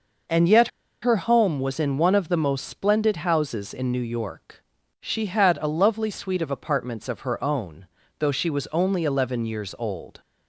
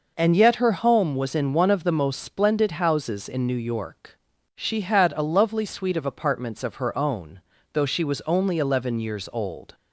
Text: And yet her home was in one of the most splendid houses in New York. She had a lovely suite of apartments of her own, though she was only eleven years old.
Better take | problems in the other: second | pauses between "yet" and "her"; slight; at 0.6 s; 0.34 s long

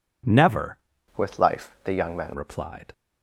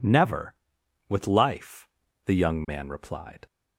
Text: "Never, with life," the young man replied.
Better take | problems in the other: second | changes voice from "with" to "man"; from 1.1 to 2.3 s; 1.2 s long

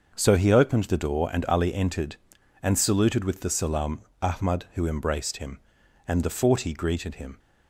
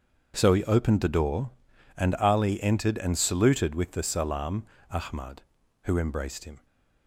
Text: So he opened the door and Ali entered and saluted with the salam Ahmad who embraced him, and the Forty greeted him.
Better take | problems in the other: first | starts louder than the rest; until 1.3 s; 7 dB; also in the first // pauses between "salam" and "Ahmad"; slight; at 4.6 s; 0.26 s long; slight in the first // stops before "and the Forty greeted him"; at 6.6 s

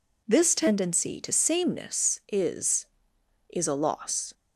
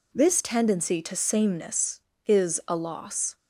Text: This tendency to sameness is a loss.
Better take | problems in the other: second | says "is" twice; at 3.4 s

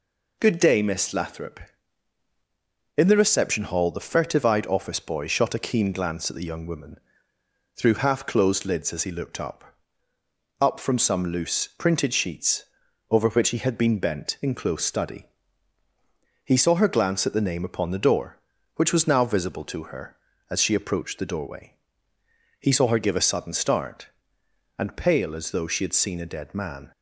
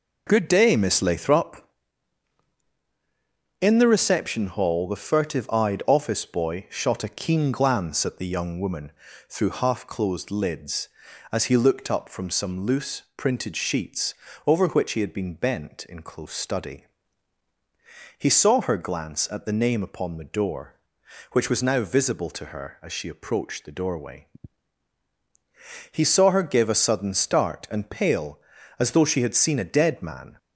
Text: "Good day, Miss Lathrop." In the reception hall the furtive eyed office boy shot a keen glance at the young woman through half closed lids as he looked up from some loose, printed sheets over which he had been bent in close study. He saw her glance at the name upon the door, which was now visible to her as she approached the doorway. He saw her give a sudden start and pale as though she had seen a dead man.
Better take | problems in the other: second | pauses between "woman" and "through"; noticeable; at 6.9 s; 0.76 s long; also in the second // says "up" twice; at 10.6 s // pauses between "sheets" and "over"; at 12.6 s; 0.44 s long; slight in the second

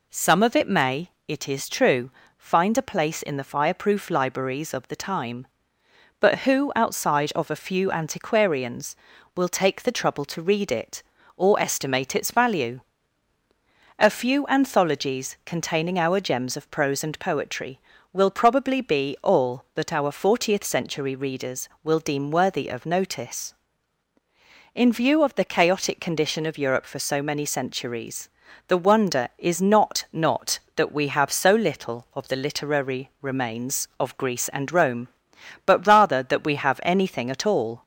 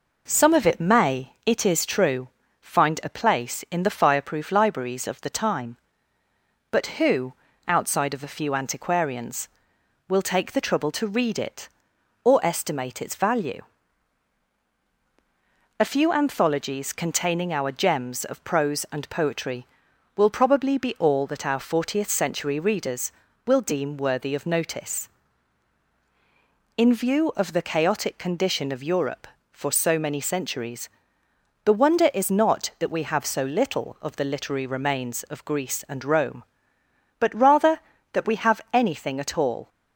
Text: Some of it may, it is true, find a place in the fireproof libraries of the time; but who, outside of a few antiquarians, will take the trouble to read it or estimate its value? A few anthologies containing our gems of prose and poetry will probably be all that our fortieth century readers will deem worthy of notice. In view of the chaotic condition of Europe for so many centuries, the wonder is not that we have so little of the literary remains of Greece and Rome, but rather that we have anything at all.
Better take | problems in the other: second | says "not" twice; at 30.1 s

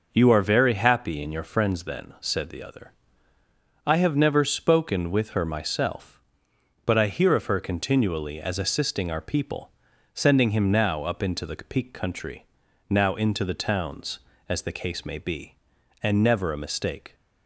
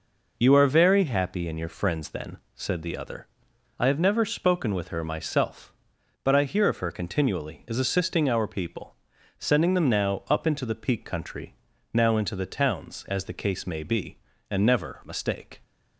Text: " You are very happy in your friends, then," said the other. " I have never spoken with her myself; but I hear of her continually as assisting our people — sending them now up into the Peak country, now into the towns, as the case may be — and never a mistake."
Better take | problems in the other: second | says "him" for "them"; at 10.5 s

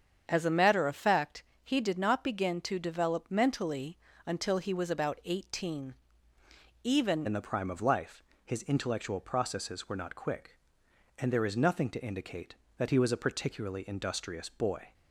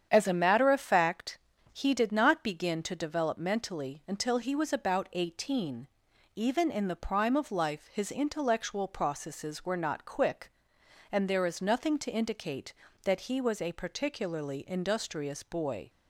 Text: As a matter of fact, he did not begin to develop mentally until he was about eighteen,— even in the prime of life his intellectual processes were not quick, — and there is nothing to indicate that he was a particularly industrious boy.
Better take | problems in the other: second | starts louder than the rest; strong; until 1.2 s; 7.5 dB; strong in the second // pauses between "mentally" and "until"; slight; at 3.9 s; 0.28 s long // changes voice at "in"; from 7.2 s on; 7.7 s long // pauses between "life" and "his"; slight; at 8.2 s; 0.20 s long

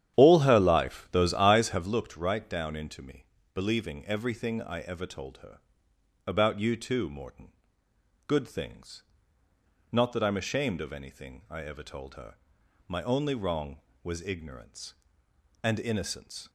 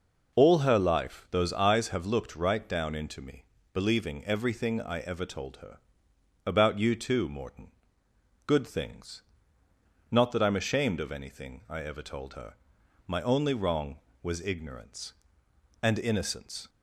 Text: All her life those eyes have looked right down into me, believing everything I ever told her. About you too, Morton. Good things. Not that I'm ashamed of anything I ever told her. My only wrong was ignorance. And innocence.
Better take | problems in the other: second | starts louder than the rest; strong; until 2.0 s; 10 dB

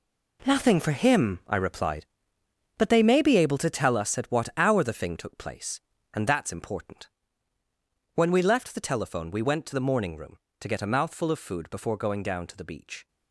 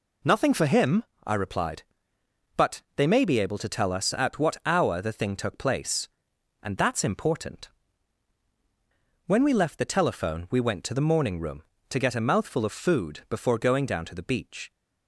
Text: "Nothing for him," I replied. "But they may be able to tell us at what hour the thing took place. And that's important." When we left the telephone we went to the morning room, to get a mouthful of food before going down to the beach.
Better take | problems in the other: second | gets quieter; strong; throughout; 11.5 dB

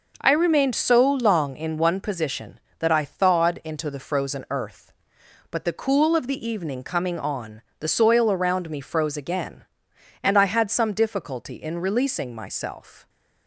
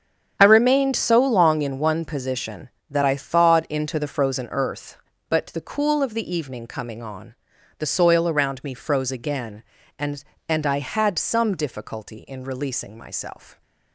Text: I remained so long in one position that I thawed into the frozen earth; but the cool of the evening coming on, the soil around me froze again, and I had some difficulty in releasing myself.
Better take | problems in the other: first | starts louder than the rest; strong; until 1.4 s; 8.5 dB // says "and" twice; at 10.4 s

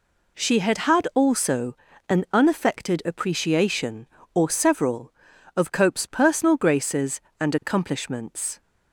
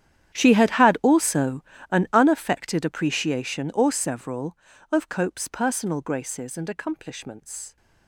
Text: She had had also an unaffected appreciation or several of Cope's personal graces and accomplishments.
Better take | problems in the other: first | gets quieter; strong; throughout; 19.5 dB // pauses between "also" and "an"; slight; at 1.6 s; 0.28 s long; slight in the first

